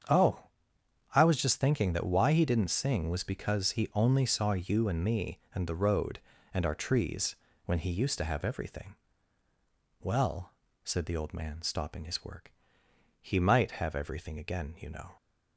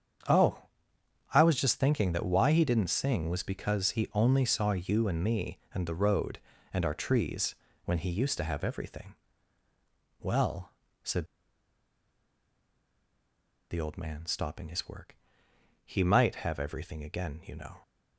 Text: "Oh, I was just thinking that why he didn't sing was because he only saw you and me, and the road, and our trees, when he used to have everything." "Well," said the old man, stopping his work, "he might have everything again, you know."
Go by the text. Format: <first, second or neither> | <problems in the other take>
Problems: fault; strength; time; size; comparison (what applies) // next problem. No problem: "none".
first | starts louder than the rest; strong; until 1.9 s; 8 dB; strong in the first // pauses between "said" and "the"; strong; at 11.2 s; 2.4 s long